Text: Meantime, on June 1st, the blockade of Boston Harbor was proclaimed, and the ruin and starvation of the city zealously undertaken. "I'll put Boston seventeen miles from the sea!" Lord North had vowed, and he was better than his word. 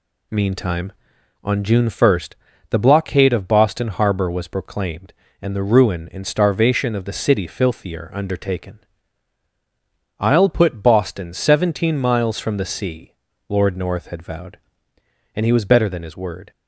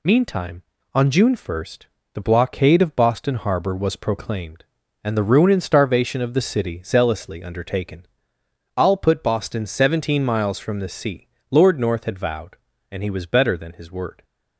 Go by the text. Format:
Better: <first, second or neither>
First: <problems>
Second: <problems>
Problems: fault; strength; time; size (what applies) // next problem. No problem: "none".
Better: second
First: says "filthier" for "zealously"; at 7.4 s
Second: none